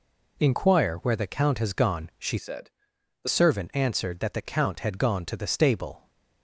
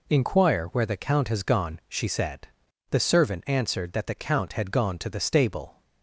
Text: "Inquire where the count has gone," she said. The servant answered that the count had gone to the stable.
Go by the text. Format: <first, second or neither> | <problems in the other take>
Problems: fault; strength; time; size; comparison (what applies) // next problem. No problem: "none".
second | changes voice from "said" to "The"; from 2.3 to 3.2 s; 0.9 s long